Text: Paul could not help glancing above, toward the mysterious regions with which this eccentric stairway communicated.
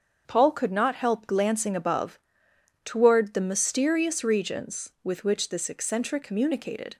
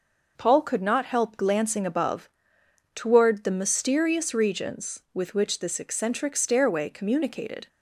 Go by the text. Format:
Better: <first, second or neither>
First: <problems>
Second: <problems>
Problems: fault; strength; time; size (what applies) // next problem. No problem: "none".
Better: second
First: starts louder than the rest; until 1.2 s; 7 dB // skips "stairway"; at 6.2 s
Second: none